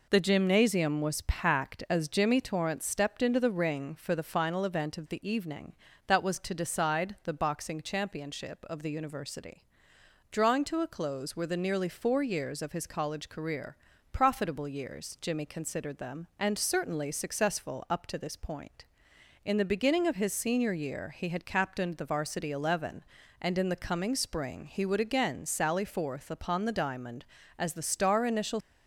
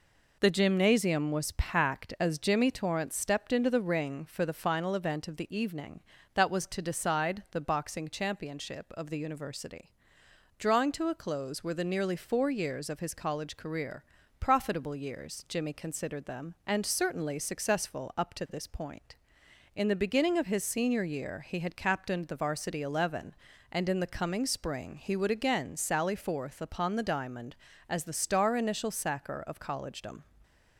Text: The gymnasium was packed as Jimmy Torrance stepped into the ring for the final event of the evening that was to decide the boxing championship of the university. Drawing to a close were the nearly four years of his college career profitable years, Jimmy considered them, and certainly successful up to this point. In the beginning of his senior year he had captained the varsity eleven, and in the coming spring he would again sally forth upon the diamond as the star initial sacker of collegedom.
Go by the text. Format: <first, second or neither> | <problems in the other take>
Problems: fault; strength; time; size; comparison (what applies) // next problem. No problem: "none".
second | pauses between "career" and "profitable"; slight; at 13.7 s; 0.34 s long; slight in the second // stops before "sacker of collegedom"; at 28.6 s